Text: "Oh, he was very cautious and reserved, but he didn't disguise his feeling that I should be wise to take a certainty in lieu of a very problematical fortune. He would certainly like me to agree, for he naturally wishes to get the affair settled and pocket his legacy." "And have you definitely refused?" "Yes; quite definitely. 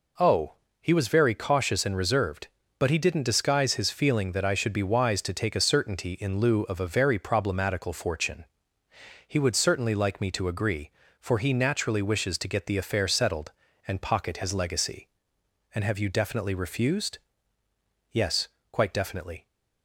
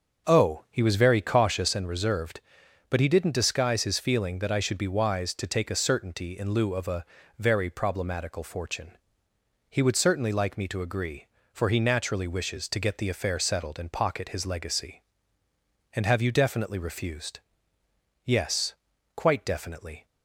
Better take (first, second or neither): first